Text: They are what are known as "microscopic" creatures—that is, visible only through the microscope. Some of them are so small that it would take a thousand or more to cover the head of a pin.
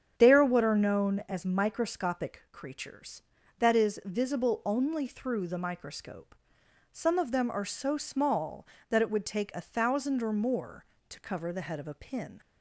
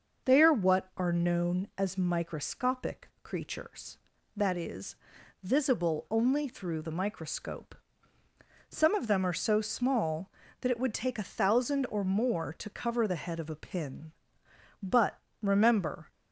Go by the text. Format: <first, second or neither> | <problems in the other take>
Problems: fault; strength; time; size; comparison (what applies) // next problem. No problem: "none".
first | starts louder than the rest; noticeable; until 1.3 s; 6 dB; strong in the first // goes on to say "But remember"; noticeable; from 14.8 s on; 1.2 s long